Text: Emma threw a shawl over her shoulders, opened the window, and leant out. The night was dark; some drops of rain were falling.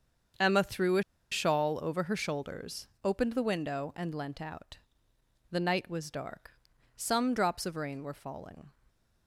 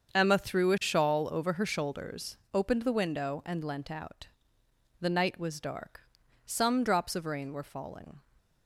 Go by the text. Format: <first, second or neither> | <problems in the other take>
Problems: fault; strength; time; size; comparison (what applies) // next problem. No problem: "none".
second | starts louder than the rest; until 1.6 s; 7 dB; also in the second // pauses between "a" and "shawl"; slight; at 1.0 s; 0.28 s long